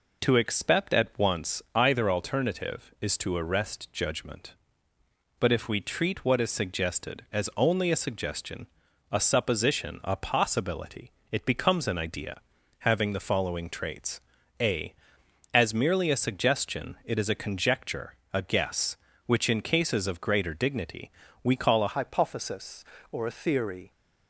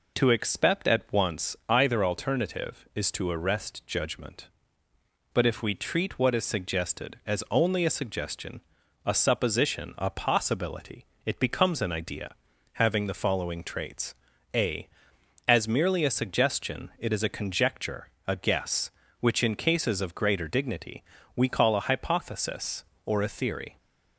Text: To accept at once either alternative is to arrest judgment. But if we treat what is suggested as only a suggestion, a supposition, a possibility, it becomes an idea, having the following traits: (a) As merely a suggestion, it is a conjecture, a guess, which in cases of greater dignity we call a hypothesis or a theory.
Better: second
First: pauses between "dignity" and "we"; slight; at 21.1 s; 0.32 s long // changes voice at "hypothesis"; from 21.9 s on; 2.0 s long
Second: pauses between "dignity" and "we"; slight; at 21.0 s; 0.32 s long

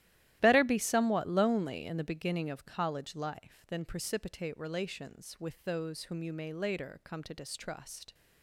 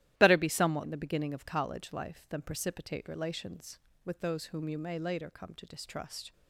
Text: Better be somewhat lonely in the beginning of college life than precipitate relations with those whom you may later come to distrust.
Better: first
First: starts louder than the rest; strong; until 1.4 s; 14 dB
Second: starts louder than the rest; strong; until 1.1 s; 14 dB // skips "lonely"; at 0.8 s

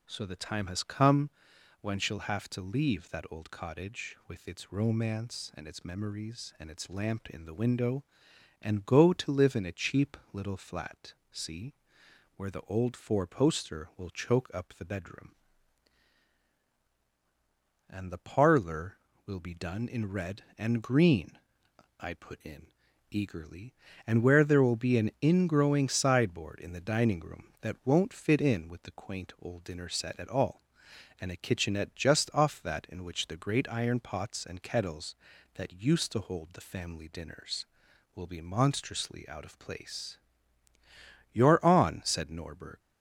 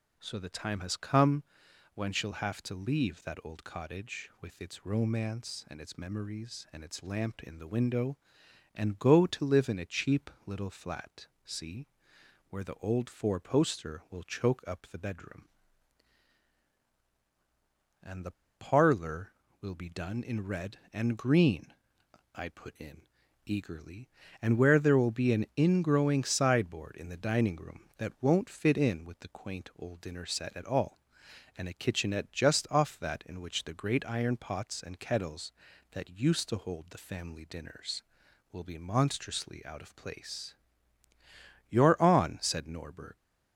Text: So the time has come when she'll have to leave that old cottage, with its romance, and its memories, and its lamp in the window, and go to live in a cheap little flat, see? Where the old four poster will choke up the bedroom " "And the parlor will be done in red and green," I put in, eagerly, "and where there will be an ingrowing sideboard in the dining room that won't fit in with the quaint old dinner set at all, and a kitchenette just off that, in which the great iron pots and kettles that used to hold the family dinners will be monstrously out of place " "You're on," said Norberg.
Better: first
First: pauses between "come" and "when"; noticeable; at 1.3 s; 0.50 s long // pauses between "cheap" and "little"; slight; at 10.1 s; 0.16 s long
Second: pauses between "come" and "when"; noticeable; at 1.4 s; 0.50 s long // pauses between "cheap" and "little"; slight; at 10.2 s; 0.16 s long // pauses between "the" and "parlor"; slight; at 18.3 s; 0.24 s long

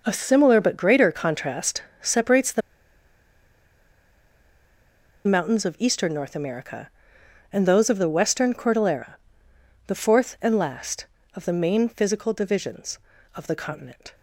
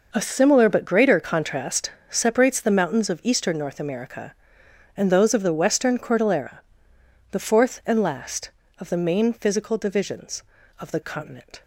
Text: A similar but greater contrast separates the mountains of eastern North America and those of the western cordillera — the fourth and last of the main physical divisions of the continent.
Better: second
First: pauses between "contrast" and "separates"; slight; at 1.8 s; 0.18 s long // pauses between "the" and "mountains"; strong; at 2.6 s; 2.6 s long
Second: pauses between "contrast" and "separates"; slight; at 1.9 s; 0.18 s long

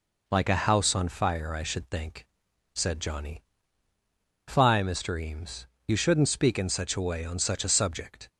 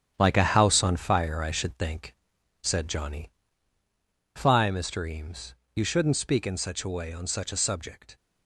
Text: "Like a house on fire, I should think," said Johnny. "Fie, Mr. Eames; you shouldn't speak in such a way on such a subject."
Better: first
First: none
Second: gets quieter; strong; throughout; 8 dB

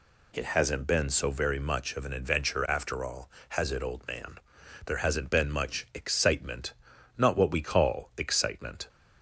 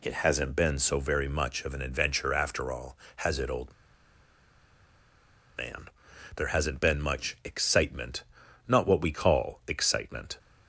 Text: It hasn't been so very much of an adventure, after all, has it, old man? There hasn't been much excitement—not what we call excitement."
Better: first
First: none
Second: pauses between "old" and "man"; strong; at 3.7 s; 1.8 s long

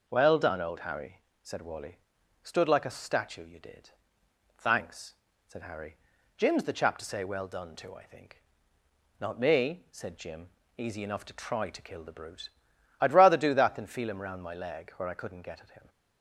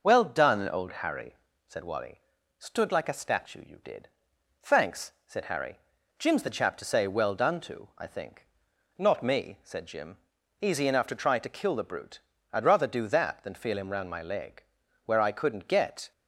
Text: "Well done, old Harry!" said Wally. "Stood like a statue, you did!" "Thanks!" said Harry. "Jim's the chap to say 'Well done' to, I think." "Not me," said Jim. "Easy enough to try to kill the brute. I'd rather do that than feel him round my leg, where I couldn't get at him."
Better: first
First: none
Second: stops before "at him"; at 16.1 s

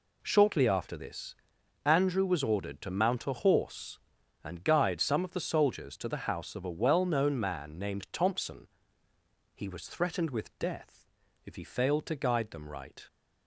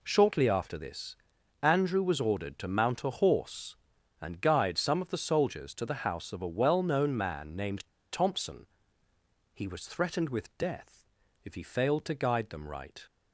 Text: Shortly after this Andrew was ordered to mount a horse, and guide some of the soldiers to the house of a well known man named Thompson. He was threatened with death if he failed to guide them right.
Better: first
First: pauses between "this" and "Andrew"; noticeable; at 1.3 s; 0.49 s long // pauses between "death" and "if"; slight; at 11.0 s; 0.36 s long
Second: pauses between "this" and "Andrew"; noticeable; at 1.1 s; 0.46 s long // pauses between "named" and "Thompson"; slight; at 7.8 s; 0.23 s long // pauses between "death" and "if"; slight; at 11.0 s; 0.36 s long

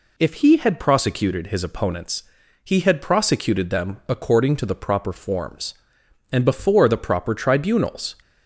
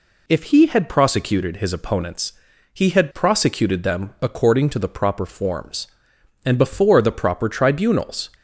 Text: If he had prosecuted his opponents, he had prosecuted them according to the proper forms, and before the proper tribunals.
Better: neither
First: none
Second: none

